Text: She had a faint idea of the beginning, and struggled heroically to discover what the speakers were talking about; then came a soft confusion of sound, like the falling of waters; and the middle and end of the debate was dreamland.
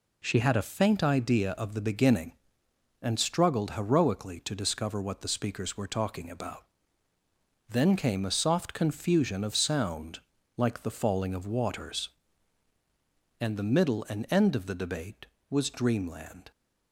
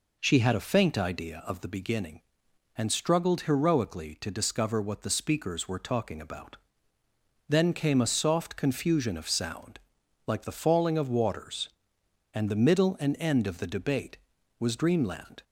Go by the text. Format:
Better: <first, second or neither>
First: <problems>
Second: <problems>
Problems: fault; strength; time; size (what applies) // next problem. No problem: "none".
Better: neither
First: none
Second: none